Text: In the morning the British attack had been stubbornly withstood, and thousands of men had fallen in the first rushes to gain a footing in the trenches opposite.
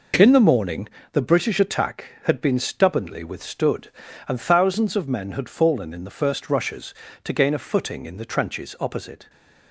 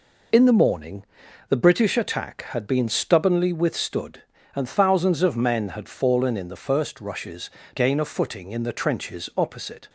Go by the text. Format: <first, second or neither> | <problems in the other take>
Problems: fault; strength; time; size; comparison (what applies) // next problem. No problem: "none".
first | pauses between "morning" and "the"; noticeable; at 1.0 s; 0.46 s long; slight in the first // skips "to"; at 7.6 s